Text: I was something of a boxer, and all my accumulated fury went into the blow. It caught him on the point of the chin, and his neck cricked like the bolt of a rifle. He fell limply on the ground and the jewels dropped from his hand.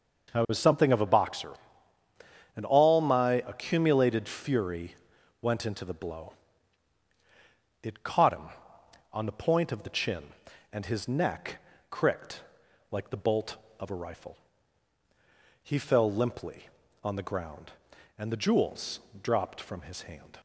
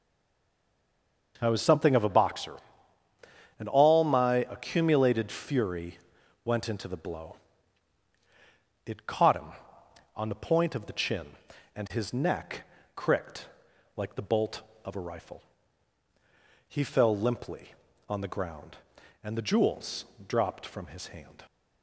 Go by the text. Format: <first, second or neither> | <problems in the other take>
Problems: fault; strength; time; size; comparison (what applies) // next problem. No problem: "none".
first | stays silent before the first word; noticeable; until 1.3 s; 1.3 s long // pauses between "fury" and "went"; noticeable; at 5.9 s; 0.46 s long; noticeable in the first // pauses between "neck" and "cricked"; slight; at 12.6 s; 0.32 s long; slight in the first // pauses between "cricked" and "like"; noticeable; at 13.4 s; 0.48 s long; noticeable in the first // pauses between "jewels" and "dropped"; slight; at 20.0 s; 0.22 s long; slight in the first